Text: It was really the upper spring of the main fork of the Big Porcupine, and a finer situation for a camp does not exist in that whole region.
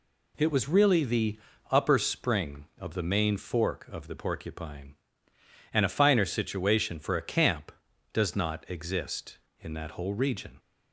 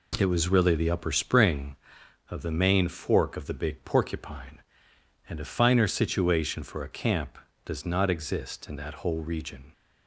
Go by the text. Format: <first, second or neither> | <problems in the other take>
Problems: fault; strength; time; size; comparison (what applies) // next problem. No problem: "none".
second | pauses between "the" and "upper"; slight; at 1.3 s; 0.34 s long // skips "Big"; at 4.1 s